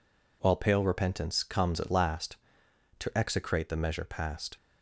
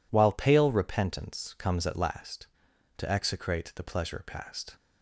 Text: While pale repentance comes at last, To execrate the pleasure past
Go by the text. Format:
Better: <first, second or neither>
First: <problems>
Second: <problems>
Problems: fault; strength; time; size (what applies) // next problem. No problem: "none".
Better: second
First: says "measure" for "pleasure"; at 3.7 s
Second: none